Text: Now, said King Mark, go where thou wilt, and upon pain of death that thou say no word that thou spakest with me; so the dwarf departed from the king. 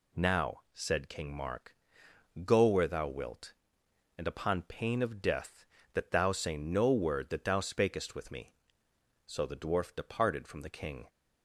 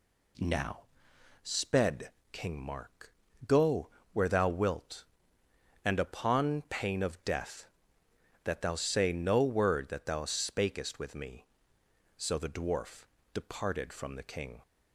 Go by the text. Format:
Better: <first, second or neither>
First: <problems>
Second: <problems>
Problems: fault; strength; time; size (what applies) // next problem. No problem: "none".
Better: first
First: none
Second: says "sped" for "said"; at 1.4 s // pauses between "go" and "where"; slight; at 3.8 s; 0.24 s long // pauses between "dwarf" and "departed"; slight; at 13.0 s; 0.26 s long